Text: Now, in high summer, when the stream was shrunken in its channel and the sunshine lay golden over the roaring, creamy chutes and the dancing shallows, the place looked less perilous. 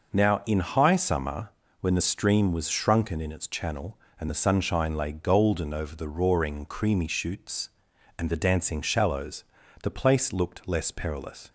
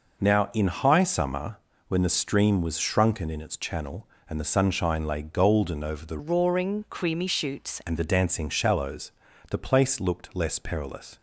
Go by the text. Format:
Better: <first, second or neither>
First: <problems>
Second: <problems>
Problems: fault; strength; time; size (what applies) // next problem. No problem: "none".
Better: first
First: none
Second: changes voice from "roaring" to "chutes"; from 6.1 to 7.8 s; 1.7 s long